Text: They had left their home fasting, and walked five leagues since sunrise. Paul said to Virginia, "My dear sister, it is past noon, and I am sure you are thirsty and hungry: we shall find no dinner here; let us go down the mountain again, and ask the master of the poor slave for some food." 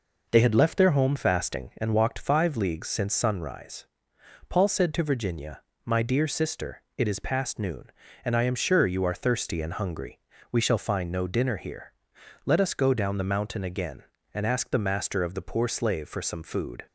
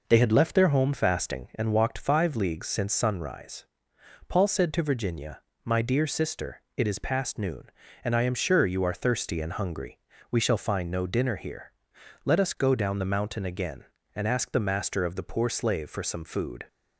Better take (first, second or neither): neither